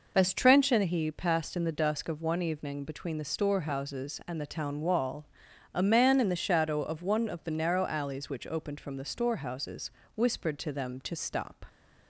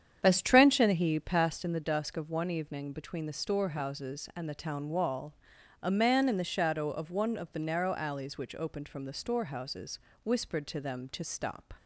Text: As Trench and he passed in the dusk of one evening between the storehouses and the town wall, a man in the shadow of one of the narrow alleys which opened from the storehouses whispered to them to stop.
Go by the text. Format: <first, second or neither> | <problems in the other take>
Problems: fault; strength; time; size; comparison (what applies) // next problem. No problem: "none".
first | starts louder than the rest; strong; until 1.7 s; 8.5 dB // pauses between "storehouses" and "whispered"; slight; at 9.9 s; 0.24 s long; slight in the first